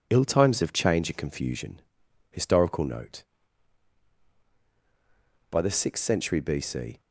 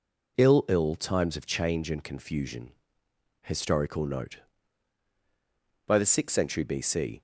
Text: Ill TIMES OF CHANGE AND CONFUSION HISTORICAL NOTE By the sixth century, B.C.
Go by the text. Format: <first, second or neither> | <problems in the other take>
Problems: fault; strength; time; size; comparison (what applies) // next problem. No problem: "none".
first | says "Ill" twice; at 0.6 s // pauses between "CONFUSION" and "HISTORICAL"; noticeable; at 2.7 s; 0.72 s long; noticeable in the first